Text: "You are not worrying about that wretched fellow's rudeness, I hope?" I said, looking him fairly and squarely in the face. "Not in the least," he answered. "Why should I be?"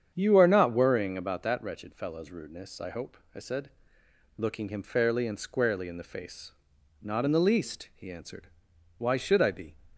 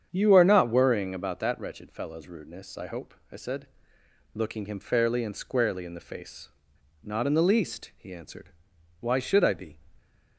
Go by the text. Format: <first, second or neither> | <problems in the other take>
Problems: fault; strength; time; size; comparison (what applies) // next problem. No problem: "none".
neither | starts louder than the rest; strong; the same in both